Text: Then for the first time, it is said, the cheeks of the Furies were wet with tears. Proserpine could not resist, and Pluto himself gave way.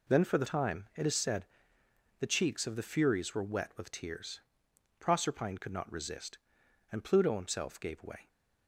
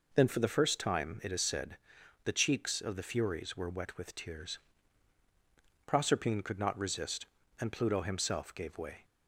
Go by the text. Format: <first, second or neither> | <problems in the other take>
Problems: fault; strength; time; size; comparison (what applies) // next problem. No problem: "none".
second | skips "first"; at 0.4 s